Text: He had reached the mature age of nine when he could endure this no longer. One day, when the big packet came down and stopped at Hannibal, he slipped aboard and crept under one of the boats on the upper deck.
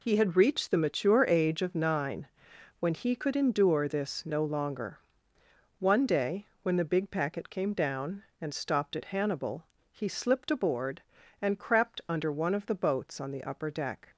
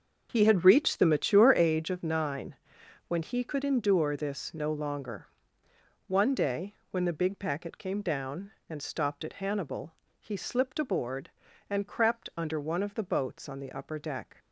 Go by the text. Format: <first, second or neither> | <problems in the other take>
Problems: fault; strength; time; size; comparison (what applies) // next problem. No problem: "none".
first | starts louder than the rest; until 1.7 s; 6.5 dB // pauses between "nine" and "when"; noticeable; at 2.5 s; 0.54 s long; noticeable in the first